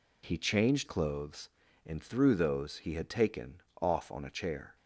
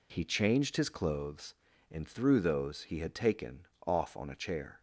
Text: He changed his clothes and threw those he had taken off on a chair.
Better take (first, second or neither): second